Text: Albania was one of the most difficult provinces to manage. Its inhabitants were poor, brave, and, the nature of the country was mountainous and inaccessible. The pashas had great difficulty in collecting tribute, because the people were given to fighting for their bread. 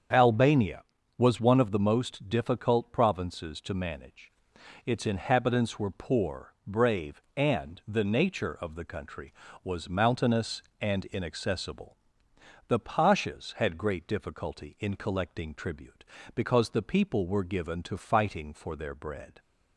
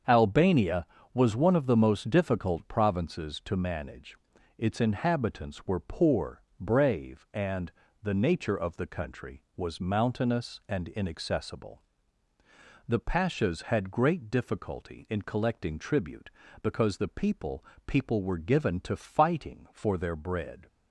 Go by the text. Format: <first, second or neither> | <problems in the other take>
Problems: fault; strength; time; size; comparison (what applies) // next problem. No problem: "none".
first | starts louder than the rest; strong; until 1.3 s; 7 dB; strong in the first // says "people" twice; at 17.8 s